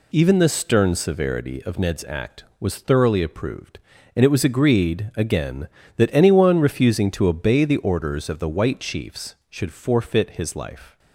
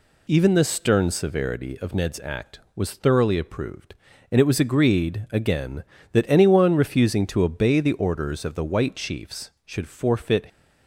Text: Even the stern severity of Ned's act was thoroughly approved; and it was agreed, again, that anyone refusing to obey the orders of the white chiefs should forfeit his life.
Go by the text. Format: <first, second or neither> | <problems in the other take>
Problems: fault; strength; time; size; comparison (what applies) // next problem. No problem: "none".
first | stops before "his life"; at 10.4 s